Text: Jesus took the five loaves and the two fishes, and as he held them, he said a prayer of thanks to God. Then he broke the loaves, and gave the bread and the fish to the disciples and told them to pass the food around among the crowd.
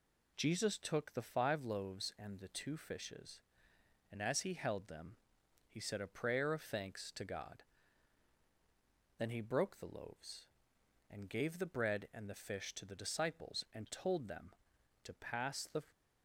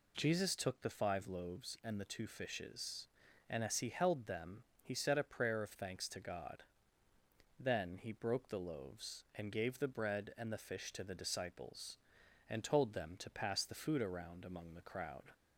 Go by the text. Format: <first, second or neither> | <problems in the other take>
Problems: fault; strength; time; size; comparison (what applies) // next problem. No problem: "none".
second | stops before "food around among the crowd"; at 15.9 s